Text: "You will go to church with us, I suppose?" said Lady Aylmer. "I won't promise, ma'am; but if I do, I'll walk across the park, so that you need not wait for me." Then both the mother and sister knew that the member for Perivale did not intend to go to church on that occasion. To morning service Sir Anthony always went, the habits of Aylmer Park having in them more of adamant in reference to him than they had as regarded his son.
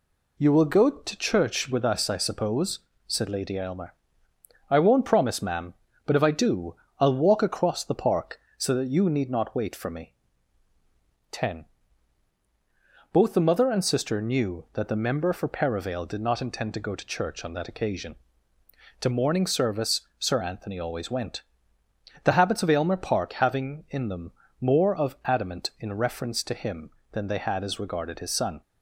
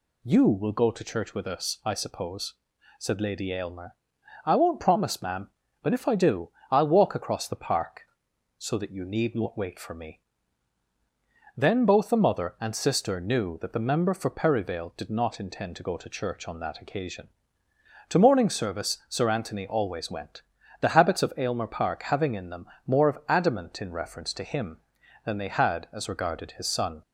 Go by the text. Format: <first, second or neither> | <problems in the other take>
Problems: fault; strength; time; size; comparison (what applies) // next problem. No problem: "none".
second | says "Ten" for "Then"; at 11.3 s // pauses between "service" and "Sir"; slight; at 20.0 s; 0.18 s long // pauses between "them" and "more"; slight; at 24.3 s; 0.28 s long; slight in the second